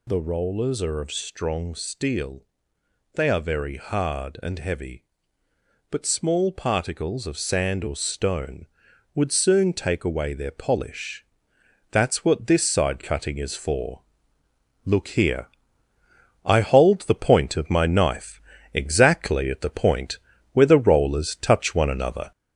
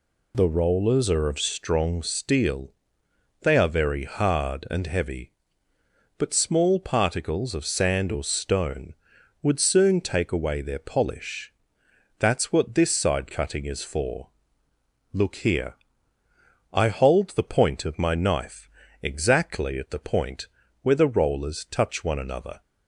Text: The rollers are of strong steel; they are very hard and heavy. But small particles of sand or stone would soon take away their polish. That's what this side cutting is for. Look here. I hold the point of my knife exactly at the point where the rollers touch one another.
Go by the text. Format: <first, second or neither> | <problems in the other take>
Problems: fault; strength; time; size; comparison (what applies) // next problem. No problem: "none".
second | gets louder; throughout; 3.5 dB // pauses between "knife" and "exactly"; slight; at 18.3 s; 0.34 s long; slight in the second // pauses between "point" and "where"; slight; at 20.1 s; 0.34 s long; slight in the second